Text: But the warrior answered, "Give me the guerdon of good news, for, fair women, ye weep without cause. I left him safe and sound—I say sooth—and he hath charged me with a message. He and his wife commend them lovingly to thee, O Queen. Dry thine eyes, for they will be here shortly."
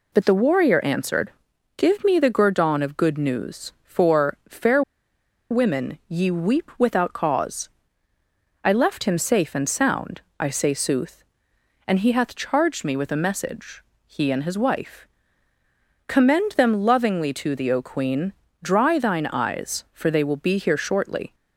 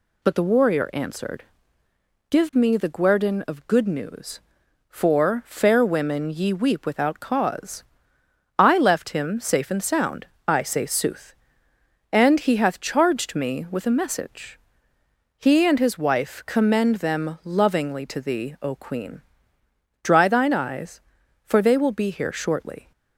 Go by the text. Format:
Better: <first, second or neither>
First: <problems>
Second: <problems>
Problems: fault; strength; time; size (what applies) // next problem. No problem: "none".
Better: second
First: pauses between "fair" and "women"; noticeable; at 4.8 s; 0.69 s long // pauses between "wife" and "commend"; at 15.0 s; 1.0 s long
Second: none